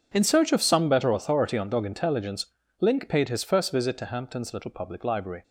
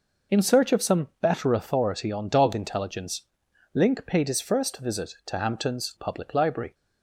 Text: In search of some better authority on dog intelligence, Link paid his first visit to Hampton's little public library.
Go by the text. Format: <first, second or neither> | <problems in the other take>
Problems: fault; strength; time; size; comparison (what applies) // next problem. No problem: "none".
first | skips "little"; at 5.9 s